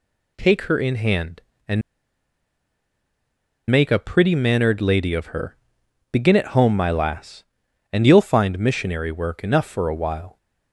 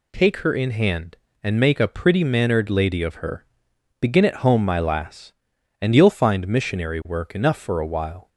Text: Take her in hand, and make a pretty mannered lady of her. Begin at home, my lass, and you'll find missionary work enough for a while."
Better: second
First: pauses between "and" and "make"; strong; at 1.8 s; 1.8 s long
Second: none

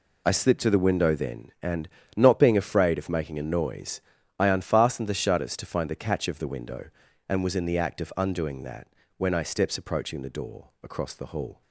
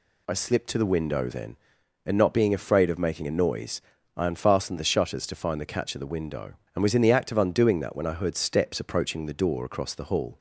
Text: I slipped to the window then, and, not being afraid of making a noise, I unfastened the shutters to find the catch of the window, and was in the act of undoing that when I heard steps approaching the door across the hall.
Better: second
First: pauses between "that" and "when"; slight; at 8.8 s; 0.30 s long // skips "heard"; at 9.4 s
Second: none

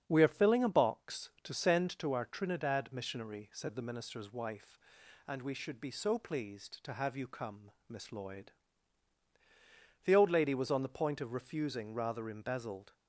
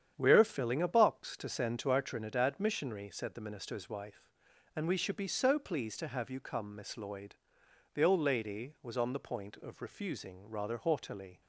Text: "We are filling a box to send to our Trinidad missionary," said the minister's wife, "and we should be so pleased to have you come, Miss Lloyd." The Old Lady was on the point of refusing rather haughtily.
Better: second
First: starts louder than the rest; strong; until 1.0 s; 8 dB // says "embezzled" for "haughtily"; at 12.2 s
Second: starts louder than the rest; strong; until 1.1 s; 9 dB

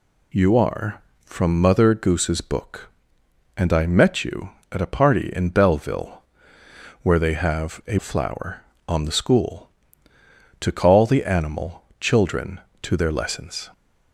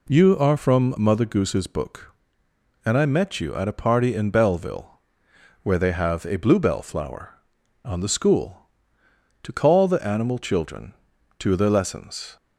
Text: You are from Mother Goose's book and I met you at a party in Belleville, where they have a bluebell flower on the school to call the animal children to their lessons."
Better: second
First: skips "bluebell"; at 7.9 s // pauses between "animal" and "children"; slight; at 11.8 s; 0.16 s long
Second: none

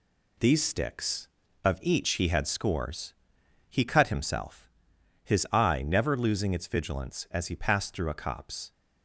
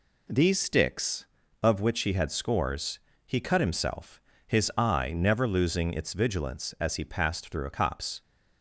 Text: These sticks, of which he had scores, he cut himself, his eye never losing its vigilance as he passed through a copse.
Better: second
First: says "each" for "which"; at 1.8 s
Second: none

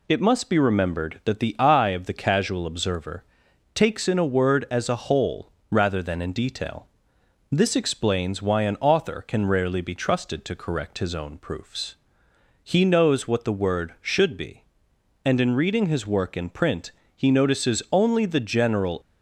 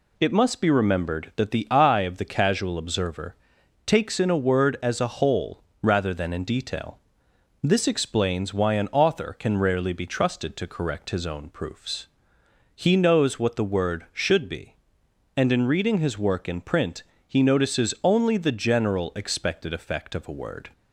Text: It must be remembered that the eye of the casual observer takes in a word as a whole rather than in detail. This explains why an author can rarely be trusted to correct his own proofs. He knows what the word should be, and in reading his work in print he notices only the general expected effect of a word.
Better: second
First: pauses between "observer" and "takes"; noticeable; at 3.2 s; 0.50 s long // pauses between "whole" and "rather"; slight; at 5.5 s; 0.20 s long // pauses between "print" and "he"; slight; at 16.9 s; 0.26 s long // stops before "expected effect of a word"; at 19.0 s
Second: pauses between "observer" and "takes"; noticeable; at 3.3 s; 0.50 s long // pauses between "whole" and "rather"; slight; at 5.6 s; 0.20 s long // pauses between "print" and "he"; slight; at 17.0 s; 0.26 s long

